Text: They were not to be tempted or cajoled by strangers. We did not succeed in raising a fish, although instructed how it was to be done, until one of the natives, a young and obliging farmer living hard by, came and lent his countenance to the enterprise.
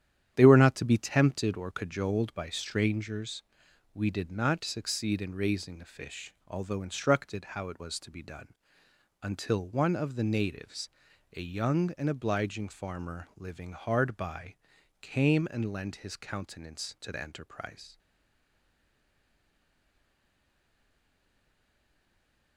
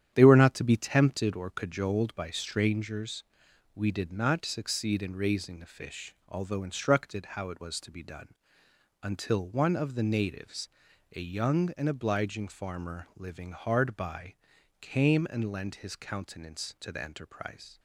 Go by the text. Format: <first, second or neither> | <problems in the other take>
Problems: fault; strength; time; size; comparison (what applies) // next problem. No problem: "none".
second | starts louder than the rest; strong; until 1.3 s; 10 dB; strong in the second // stays silent after the last word; strong; from 17.9 s on; 4.6 s long